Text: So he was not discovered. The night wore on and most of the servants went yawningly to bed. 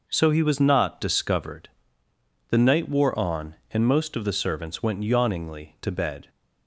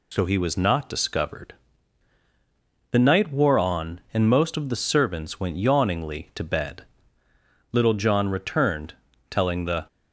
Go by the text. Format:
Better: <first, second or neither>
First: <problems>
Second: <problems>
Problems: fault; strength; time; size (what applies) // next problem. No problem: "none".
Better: first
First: none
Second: goes on to say "Little John returned telling the"; strong; from 7.7 s on; 2.1 s long